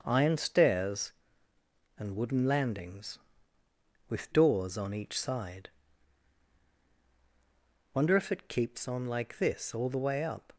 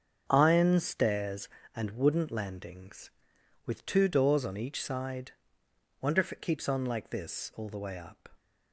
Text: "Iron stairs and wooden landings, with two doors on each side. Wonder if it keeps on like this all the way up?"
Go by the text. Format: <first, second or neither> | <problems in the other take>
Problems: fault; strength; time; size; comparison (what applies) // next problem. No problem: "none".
second | starts louder than the rest; until 1.0 s; 6.5 dB; also in the second // skips "two"; at 4.3 s